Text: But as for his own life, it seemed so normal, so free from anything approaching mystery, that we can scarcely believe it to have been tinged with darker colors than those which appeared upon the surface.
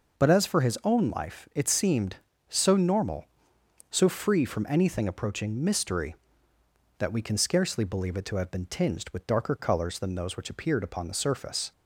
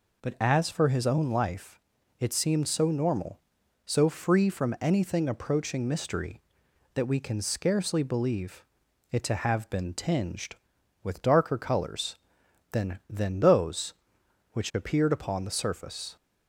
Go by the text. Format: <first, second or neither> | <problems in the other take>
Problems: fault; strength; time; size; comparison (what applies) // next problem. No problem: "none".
first | pauses between "believe" and "it"; noticeable; at 8.6 s; 0.48 s long // says "than" twice; at 13.0 s